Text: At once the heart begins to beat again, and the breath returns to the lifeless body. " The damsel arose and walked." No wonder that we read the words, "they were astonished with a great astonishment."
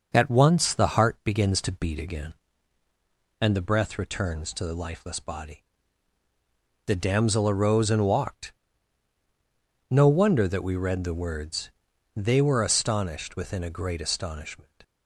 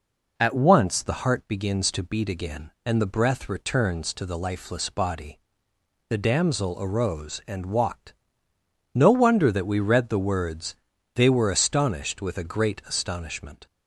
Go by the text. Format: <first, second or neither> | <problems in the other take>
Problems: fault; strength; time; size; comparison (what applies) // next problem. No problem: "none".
second | starts louder than the rest; until 1.1 s; 6.5 dB // says "within" for "with"; at 13.3 s